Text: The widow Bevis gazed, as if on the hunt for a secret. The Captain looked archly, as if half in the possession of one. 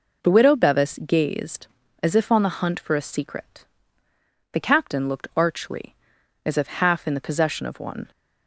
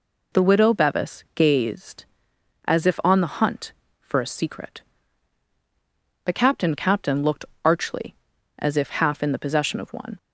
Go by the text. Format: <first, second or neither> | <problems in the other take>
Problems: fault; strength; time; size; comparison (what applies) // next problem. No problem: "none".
first | says "Captain" twice; at 6.7 s // pauses between "looked" and "archly"; slight; at 7.4 s; 0.18 s long